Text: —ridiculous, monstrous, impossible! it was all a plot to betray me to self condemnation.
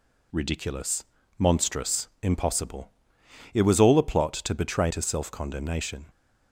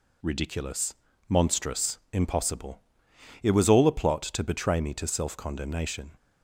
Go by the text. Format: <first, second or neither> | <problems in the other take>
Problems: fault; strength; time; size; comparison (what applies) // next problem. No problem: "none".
second | skips "me"; at 4.8 s